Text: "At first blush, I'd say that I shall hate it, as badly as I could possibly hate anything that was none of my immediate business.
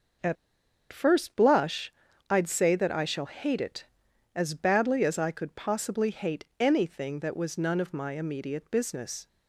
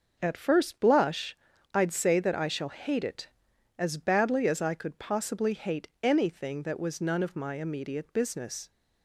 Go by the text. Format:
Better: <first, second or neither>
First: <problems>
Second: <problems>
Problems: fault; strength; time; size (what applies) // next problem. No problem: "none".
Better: second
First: pauses between "At" and "first"; noticeable; at 0.3 s; 0.55 s long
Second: none